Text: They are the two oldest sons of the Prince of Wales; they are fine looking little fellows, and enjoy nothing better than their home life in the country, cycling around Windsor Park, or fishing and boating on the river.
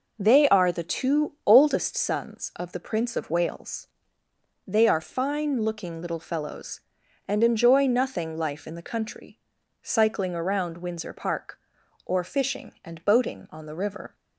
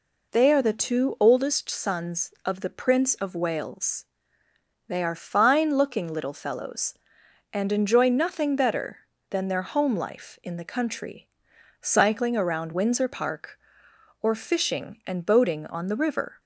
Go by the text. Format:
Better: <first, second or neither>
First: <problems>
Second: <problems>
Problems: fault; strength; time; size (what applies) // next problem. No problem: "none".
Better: second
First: skips "better than their home"; at 8.3 s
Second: none